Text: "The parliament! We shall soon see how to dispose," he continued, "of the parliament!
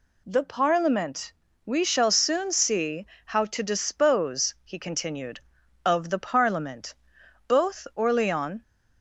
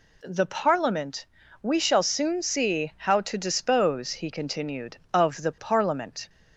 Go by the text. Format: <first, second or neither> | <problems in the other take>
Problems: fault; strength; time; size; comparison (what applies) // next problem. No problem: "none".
second | pauses between "see" and "how"; slight; at 3.0 s; 0.19 s long // goes on to say "Both Orleans"; noticeable; from 7.4 s on; 1.1 s long